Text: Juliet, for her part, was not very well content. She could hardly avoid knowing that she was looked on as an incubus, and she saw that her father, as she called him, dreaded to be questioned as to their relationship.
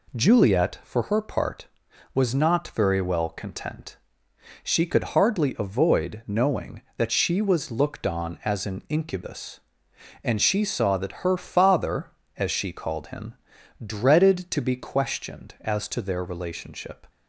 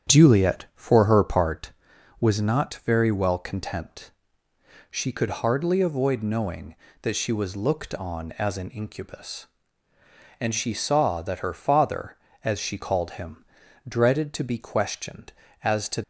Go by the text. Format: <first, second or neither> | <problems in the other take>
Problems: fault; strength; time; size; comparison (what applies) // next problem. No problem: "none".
first | starts louder than the rest; strong; until 1.1 s; 9 dB // stops before "their relationship"; at 16.0 s